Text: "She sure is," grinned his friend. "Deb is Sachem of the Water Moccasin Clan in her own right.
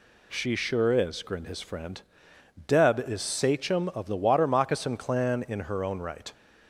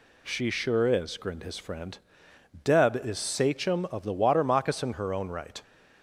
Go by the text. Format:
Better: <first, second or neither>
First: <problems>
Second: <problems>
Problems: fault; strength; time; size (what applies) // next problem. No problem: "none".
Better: first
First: none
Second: skips "Clan in"; at 4.9 s